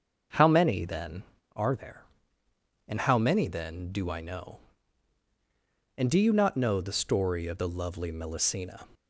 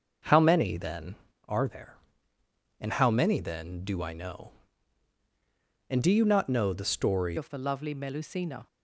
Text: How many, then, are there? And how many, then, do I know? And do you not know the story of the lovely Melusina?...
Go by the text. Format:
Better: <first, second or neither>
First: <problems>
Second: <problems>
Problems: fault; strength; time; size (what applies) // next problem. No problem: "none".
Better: first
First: starts louder than the rest; until 1.7 s; 6.5 dB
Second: starts louder than the rest; until 1.6 s; 6 dB // changes voice at "of"; from 7.3 s on; 1.3 s long